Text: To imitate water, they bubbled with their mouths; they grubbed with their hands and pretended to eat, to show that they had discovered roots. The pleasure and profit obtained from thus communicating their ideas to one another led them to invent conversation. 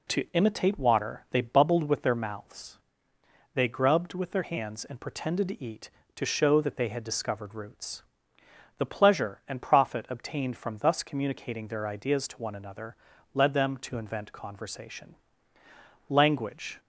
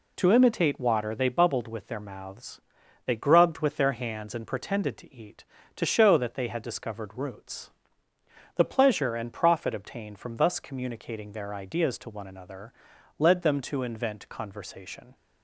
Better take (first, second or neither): second